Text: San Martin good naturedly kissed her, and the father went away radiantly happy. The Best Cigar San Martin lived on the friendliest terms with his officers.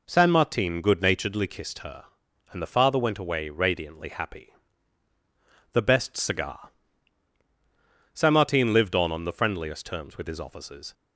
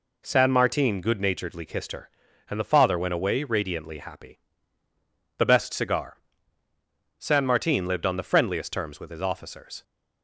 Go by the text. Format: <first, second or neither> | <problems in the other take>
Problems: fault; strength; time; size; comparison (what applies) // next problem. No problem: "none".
second | pauses between "Cigar" and "San"; strong; at 6.6 s; 1.4 s long; also in the second // says "on" twice; at 9.1 s